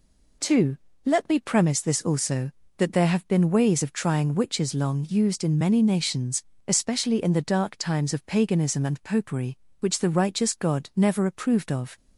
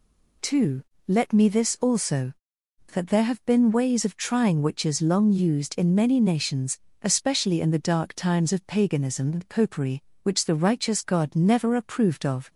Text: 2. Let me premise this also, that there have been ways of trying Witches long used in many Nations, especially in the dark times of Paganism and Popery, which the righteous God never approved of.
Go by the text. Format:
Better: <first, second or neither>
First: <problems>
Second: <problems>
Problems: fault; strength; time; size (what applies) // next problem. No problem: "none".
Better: first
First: none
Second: skips "premise"; at 1.4 s